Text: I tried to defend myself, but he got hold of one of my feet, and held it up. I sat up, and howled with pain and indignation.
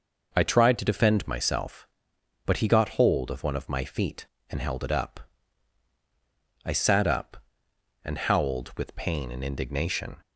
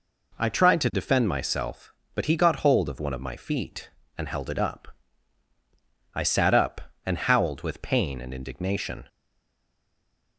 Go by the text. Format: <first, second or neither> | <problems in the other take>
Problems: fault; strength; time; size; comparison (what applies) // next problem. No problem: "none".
first | stays silent after the last word; noticeable; from 9.0 s on; 1.3 s long